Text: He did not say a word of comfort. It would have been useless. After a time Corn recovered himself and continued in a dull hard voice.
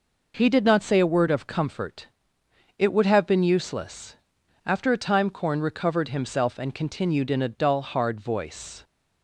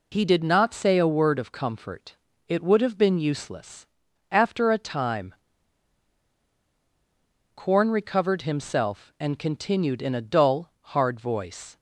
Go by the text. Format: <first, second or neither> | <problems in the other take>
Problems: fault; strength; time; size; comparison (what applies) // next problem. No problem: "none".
first | pauses between "time" and "Corn"; strong; at 5.3 s; 2.2 s long